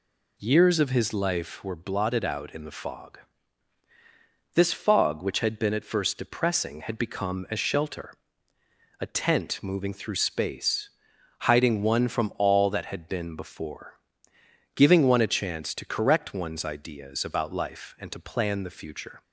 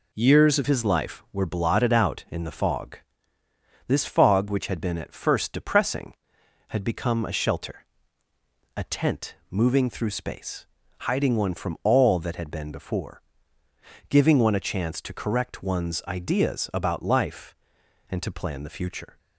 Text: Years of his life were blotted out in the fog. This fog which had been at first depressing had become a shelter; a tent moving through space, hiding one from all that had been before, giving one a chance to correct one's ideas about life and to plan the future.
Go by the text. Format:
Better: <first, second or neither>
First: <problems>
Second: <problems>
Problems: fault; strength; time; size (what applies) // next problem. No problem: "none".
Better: first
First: none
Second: changes voice at "his"; from 0.6 s on; 18.5 s long